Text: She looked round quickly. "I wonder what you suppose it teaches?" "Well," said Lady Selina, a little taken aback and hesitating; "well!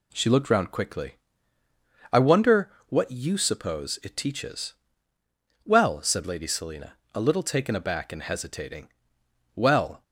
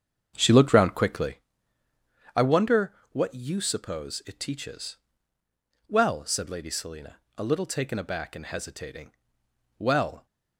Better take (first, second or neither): first